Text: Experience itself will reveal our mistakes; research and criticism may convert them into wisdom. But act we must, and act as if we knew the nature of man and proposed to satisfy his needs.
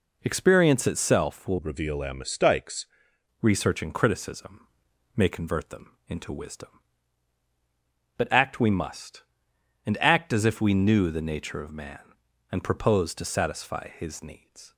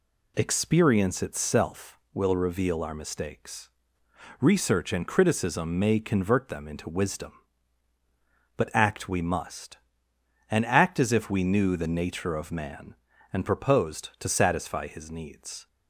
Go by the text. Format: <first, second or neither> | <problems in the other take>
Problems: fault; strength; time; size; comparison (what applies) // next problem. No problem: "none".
second | changes voice from "reveal" to "mistakes"; from 1.5 to 2.8 s; 1.3 s long // pauses between "criticism" and "may"; noticeable; at 4.6 s; 0.48 s long